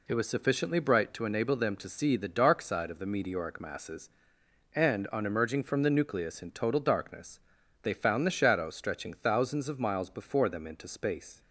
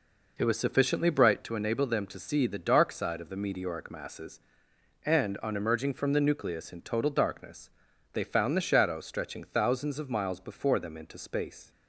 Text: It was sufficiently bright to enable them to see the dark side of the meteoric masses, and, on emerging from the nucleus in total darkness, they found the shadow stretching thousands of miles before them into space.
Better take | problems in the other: first | starts louder than the rest; noticeable; until 1.5 s; 4.5 dB

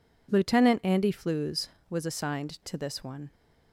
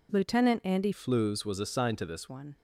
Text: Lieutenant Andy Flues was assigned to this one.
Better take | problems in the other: first | changes voice from "Flues" to "this"; from 0.9 to 2.2 s; 1.3 s long

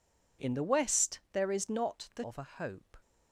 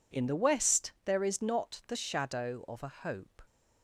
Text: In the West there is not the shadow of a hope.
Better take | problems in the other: second | skips "shadow"; at 2.2 s

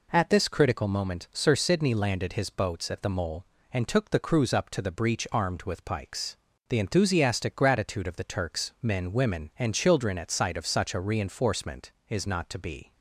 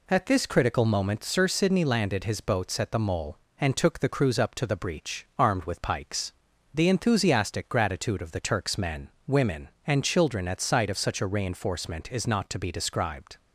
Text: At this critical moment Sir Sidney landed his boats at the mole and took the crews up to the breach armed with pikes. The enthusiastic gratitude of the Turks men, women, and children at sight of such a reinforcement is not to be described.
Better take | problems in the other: second | stops before "described"; at 12.9 s

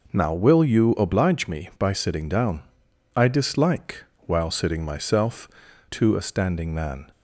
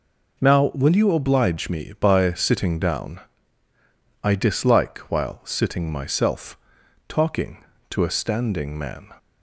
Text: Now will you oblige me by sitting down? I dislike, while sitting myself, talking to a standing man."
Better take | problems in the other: second | skips "talking"; at 5.6 s

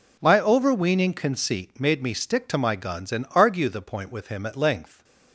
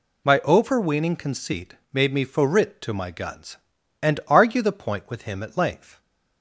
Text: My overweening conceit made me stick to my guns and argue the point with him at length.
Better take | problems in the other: first | pauses between "conceit" and "made"; slight; at 1.7 s; 0.18 s long // says "forrit" for "stick"; at 2.2 s

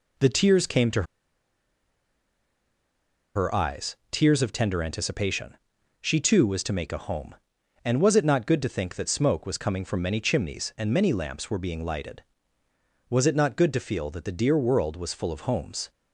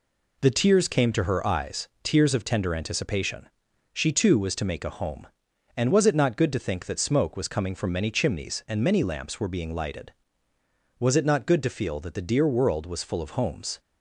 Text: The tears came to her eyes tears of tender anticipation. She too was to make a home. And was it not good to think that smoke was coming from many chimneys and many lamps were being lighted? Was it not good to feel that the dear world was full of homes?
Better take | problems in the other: second | pauses between "to" and "her"; strong; at 1.0 s; 2.3 s long

